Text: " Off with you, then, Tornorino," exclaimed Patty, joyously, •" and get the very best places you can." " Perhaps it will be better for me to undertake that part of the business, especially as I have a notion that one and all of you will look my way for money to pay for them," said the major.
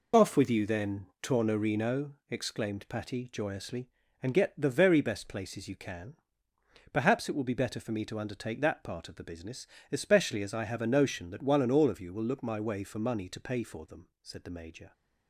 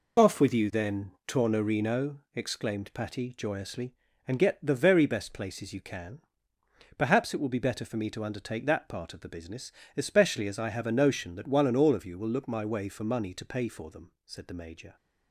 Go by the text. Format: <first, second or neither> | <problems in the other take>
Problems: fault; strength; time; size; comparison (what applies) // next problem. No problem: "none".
neither | none